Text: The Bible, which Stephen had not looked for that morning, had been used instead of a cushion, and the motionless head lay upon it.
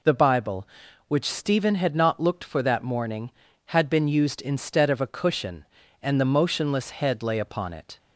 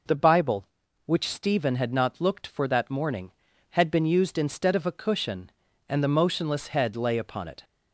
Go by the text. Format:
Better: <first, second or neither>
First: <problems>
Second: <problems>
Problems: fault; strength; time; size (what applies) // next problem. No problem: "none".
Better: neither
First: none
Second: none